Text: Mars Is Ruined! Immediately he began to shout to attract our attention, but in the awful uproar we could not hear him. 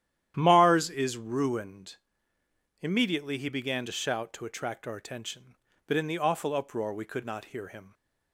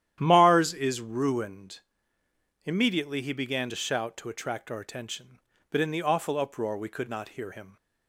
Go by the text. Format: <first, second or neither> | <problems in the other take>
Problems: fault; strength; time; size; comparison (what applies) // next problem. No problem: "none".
neither | starts louder than the rest; strong; the same in both